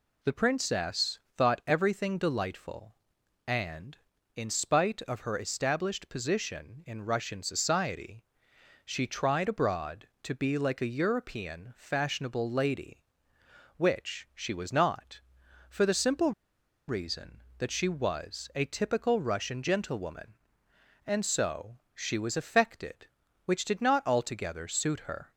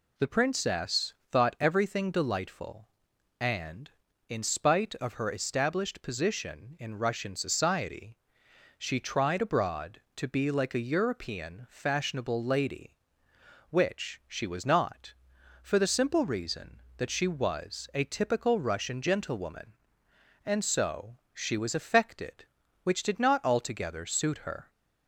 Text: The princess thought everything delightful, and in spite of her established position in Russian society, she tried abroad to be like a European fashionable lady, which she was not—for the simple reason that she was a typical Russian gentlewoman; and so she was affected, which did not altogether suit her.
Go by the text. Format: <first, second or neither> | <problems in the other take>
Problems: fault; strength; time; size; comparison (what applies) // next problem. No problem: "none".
second | pauses between "princess" and "thought"; slight; at 1.1 s; 0.18 s long; slight in the second // pauses between "simple" and "reason"; noticeable; at 16.3 s; 0.56 s long // pauses between "so" and "she"; slight; at 21.7 s; 0.16 s long; slight in the second